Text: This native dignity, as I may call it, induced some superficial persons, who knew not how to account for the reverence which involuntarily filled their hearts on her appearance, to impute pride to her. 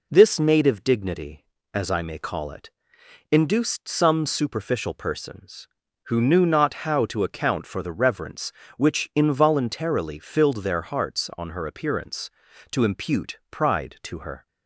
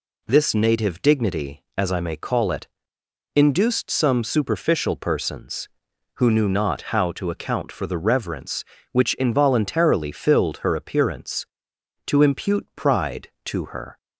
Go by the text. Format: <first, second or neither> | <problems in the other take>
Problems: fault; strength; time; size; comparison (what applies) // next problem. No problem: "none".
first | skips "their hearts on"; at 10.5 s